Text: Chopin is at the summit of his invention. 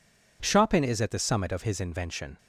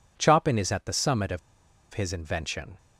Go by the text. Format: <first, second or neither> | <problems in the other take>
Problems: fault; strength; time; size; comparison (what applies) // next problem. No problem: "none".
first | pauses between "of" and "his"; noticeable; at 1.3 s; 0.53 s long